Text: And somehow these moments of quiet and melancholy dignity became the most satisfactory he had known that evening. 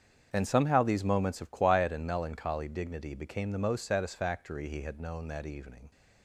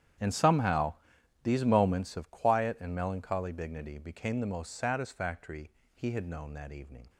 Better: first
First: starts louder than the rest; strong; until 1.3 s; 8 dB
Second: gets quieter; strong; throughout; 18.5 dB // starts louder than the rest; strong; until 1.7 s; 10 dB // pauses between "somehow" and "these"; noticeable; at 0.9 s; 0.50 s long // pauses between "satisfactory" and "he"; slight; at 5.6 s; 0.26 s long

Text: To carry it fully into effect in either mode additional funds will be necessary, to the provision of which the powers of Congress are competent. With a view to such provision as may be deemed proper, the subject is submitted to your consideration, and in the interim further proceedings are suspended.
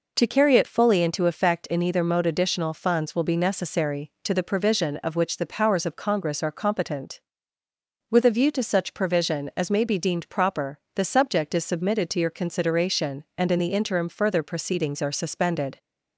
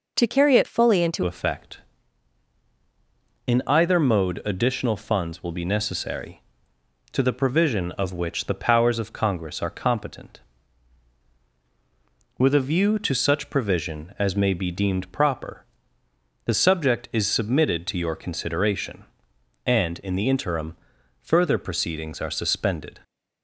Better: first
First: none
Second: changes voice at "effect"; from 1.2 s on; 21.7 s long // pauses between "interim" and "further"; noticeable; at 20.7 s; 0.48 s long

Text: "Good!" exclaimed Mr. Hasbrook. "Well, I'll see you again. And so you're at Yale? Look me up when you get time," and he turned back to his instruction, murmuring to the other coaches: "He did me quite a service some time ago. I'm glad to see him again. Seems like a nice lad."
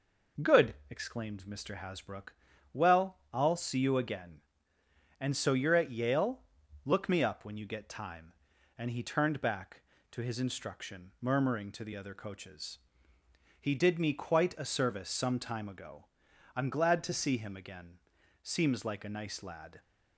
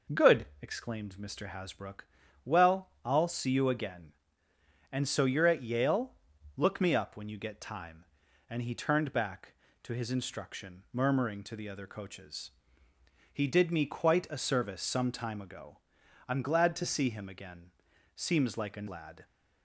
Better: first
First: none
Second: skips "nice"; at 18.8 s

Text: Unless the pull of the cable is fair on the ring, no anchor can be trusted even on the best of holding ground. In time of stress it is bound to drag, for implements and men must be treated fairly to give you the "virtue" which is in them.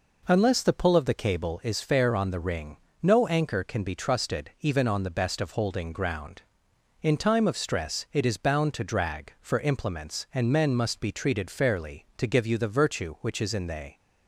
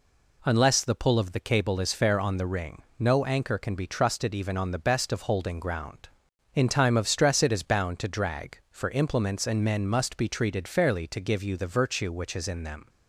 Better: second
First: says "they" for "them"; at 13.6 s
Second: none

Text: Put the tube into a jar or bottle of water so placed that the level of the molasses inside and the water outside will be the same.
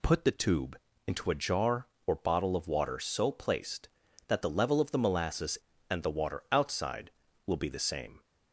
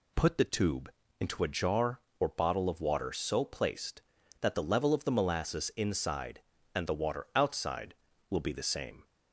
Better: second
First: pauses between "tube" and "into"; slight; at 0.7 s; 0.30 s long // skips "inside"; at 5.7 s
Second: pauses between "tube" and "into"; slight; at 0.8 s; 0.30 s long

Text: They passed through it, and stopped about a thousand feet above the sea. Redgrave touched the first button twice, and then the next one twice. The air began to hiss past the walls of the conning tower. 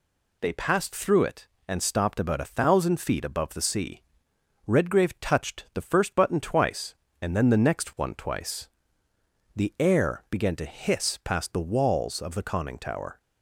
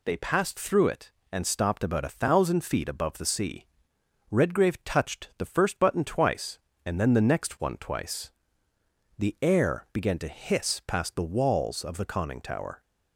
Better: neither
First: none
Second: none

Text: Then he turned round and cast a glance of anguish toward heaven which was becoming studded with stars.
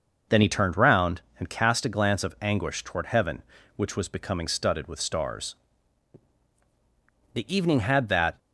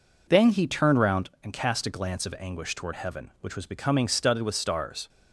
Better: second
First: goes on to say "The evening had that"; noticeable; from 7.3 s on; 1.0 s long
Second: none

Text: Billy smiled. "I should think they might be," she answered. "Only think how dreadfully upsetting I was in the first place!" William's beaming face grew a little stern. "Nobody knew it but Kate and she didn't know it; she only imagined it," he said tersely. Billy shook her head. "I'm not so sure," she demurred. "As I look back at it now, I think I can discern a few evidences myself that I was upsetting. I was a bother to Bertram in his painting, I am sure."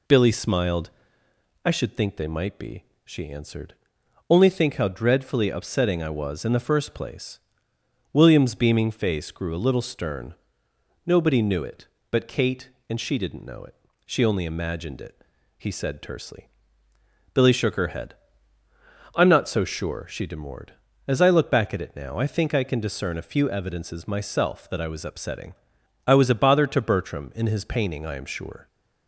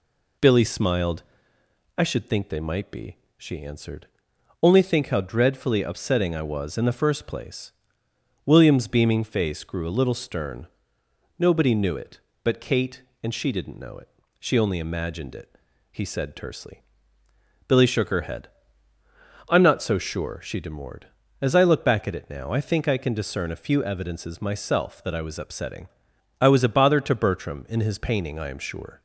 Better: neither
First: none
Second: none

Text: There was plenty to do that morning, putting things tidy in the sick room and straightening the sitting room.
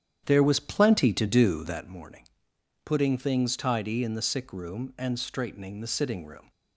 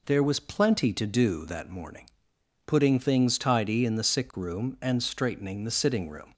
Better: second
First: starts louder than the rest; strong; until 1.9 s; 9.5 dB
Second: none

